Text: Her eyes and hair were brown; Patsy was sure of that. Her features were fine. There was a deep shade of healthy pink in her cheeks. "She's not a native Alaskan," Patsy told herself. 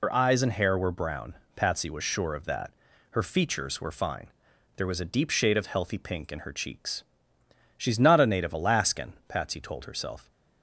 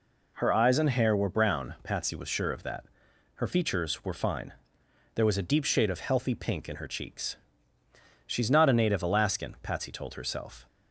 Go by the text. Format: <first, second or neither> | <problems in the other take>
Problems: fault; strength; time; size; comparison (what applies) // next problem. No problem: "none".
second | loses the start of "Her"; at 0.0 s; 85 ms